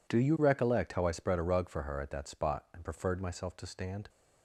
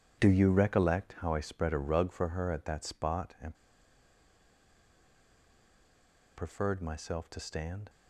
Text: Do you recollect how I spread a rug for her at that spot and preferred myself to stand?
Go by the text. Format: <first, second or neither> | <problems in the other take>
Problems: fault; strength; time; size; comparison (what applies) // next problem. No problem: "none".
first | pauses between "and" and "preferred"; strong; at 3.5 s; 2.8 s long